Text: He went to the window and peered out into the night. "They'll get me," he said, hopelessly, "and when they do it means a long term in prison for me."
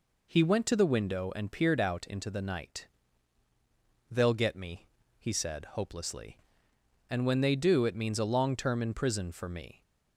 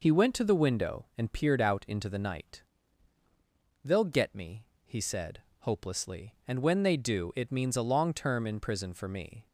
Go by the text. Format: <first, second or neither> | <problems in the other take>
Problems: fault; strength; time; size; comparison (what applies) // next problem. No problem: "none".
neither | none